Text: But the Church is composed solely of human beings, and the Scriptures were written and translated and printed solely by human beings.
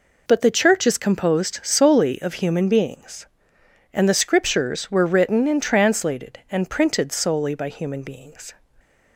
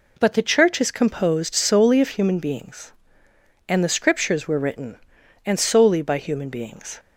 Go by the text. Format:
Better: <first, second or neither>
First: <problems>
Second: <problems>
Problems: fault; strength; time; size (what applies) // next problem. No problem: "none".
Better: first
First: none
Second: skips "translated and printed"; at 5.5 s